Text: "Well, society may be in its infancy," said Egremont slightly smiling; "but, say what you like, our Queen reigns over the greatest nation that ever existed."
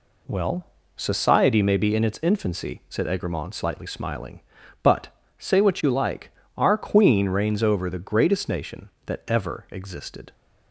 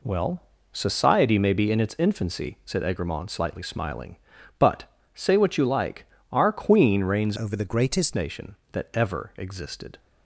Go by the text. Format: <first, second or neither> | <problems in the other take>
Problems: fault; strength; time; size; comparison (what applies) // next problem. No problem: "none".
first | changes voice from "over" to "greatest"; from 7.3 to 8.1 s; 0.8 s long